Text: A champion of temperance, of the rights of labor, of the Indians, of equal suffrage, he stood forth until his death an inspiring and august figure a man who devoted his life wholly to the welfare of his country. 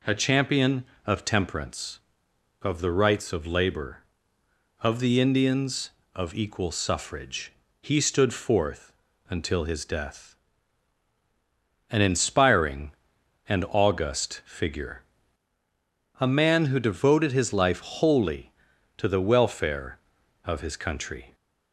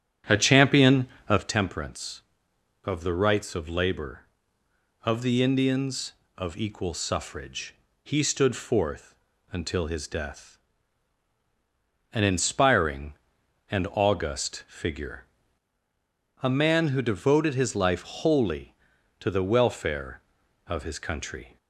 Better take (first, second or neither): first